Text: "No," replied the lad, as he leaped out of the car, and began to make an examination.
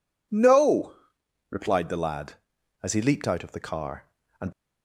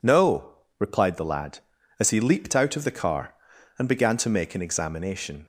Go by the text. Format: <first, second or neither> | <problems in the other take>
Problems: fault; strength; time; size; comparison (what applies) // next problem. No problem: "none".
second | stops before "began to make an examination"; at 4.5 s